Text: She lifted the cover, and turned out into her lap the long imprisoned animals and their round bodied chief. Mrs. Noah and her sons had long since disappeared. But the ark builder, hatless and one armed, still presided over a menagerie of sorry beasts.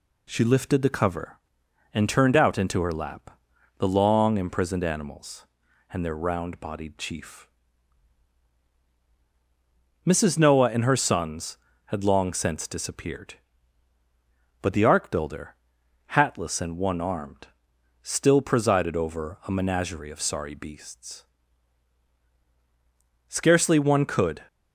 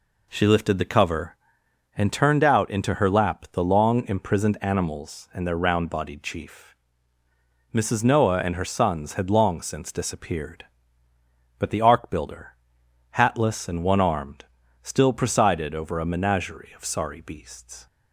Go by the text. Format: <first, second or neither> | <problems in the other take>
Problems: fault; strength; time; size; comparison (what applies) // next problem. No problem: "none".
second | pauses between "lap" and "the"; at 3.3 s; 0.42 s long // goes on to say "Scarcely one could"; noticeable; from 23.2 s on; 1.1 s long